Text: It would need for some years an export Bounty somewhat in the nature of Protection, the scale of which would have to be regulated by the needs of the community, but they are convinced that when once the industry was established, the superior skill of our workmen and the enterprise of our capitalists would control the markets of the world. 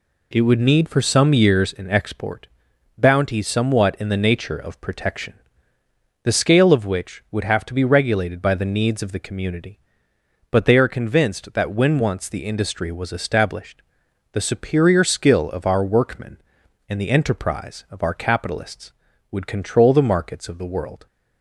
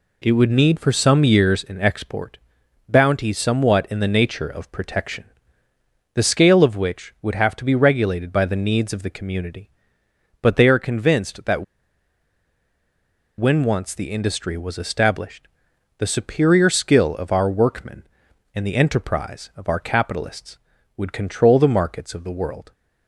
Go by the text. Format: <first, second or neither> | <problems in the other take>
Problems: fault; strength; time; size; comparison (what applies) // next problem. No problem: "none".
first | pauses between "export" and "Bounty"; noticeable; at 2.3 s; 0.50 s long; noticeable in the first // pauses between "that" and "when"; strong; at 11.6 s; 1.7 s long